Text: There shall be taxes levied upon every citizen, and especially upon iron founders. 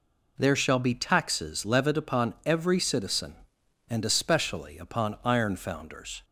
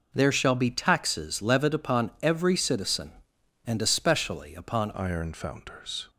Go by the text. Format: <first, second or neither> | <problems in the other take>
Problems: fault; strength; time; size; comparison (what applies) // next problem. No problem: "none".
first | changes voice at "iron"; from 4.9 s on; 1.1 s long